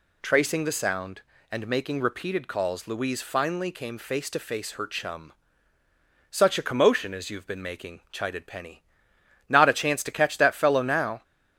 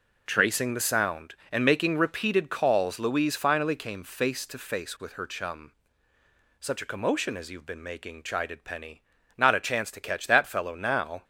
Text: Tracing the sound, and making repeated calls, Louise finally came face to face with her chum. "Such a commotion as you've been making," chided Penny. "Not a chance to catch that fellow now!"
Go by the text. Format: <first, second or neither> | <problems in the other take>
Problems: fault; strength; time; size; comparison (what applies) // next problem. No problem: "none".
second | skips "with"; at 4.7 s